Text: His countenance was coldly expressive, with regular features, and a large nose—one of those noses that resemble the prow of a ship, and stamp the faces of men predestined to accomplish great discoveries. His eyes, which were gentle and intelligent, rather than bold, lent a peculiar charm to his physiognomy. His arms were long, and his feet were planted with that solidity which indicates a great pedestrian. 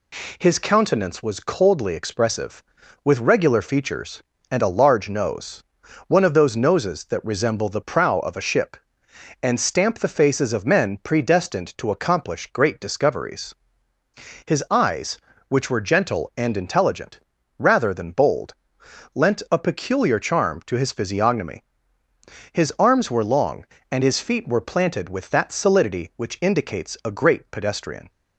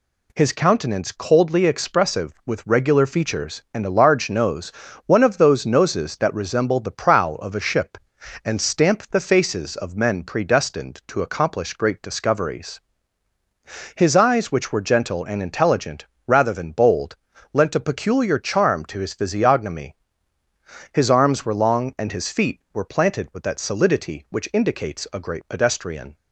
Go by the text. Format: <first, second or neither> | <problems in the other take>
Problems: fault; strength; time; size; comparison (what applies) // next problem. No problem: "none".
first | skips "was"; at 1.1 s